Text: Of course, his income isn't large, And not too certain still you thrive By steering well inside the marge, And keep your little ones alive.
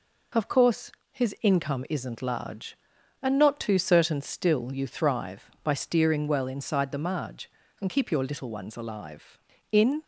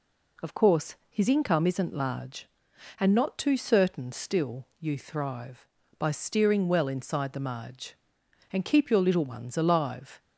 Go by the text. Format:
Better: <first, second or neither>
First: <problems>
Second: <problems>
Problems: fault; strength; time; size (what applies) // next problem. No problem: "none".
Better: second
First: goes on to say "In"; slight; from 9.7 s on; 0.32 s long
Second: none